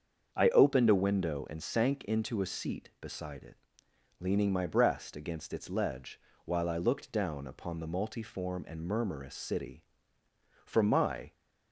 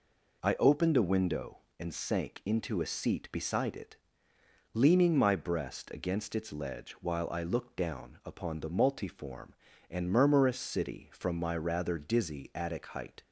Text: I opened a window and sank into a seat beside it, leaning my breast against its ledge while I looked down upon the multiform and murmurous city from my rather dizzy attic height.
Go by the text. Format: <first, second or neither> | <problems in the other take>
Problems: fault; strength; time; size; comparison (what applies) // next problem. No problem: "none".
second | starts louder than the rest; until 1.3 s; 7 dB // pauses between "ledge" and "while"; slight; at 6.1 s; 0.28 s long // stops before "rather dizzy attic height"; at 11.3 s